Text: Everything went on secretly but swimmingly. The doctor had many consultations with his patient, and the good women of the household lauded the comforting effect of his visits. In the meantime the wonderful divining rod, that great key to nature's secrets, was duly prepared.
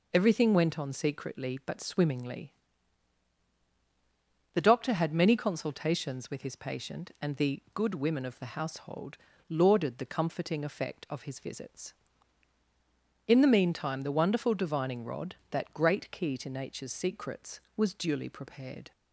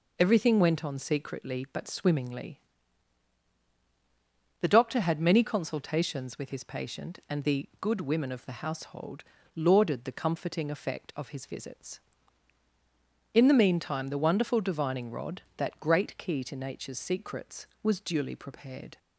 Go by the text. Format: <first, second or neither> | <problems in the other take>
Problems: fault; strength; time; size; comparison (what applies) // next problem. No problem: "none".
neither | pauses between "household" and "lauded"; slight; the same in both